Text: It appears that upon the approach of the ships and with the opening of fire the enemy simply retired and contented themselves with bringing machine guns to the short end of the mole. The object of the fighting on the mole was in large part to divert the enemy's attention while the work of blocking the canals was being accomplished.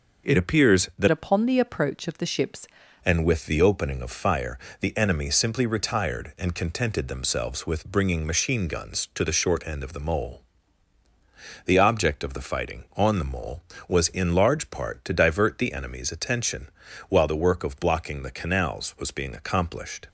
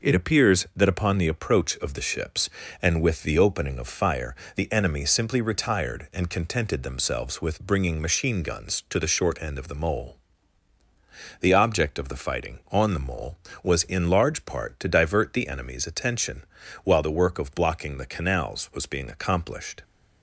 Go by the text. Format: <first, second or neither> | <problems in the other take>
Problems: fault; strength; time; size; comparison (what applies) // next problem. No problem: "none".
second | starts louder than the rest; until 1.3 s; 6 dB // changes voice from "upon" to "ships"; from 1.0 to 2.6 s; 1.6 s long // pauses between "fire" and "the"; slight; at 4.5 s; 0.22 s long; slight in the second // pauses between "attention" and "while"; at 16.6 s; 0.40 s long; also in the second